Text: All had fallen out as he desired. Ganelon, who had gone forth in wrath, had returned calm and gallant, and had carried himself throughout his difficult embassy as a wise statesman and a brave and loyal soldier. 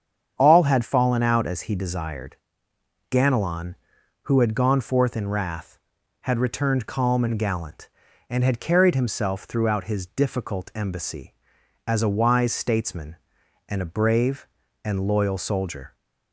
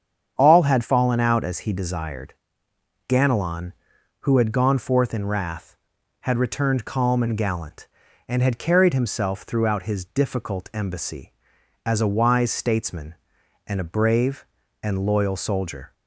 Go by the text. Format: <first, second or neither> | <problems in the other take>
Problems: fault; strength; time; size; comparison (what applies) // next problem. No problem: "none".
neither | starts louder than the rest; strong; the same in both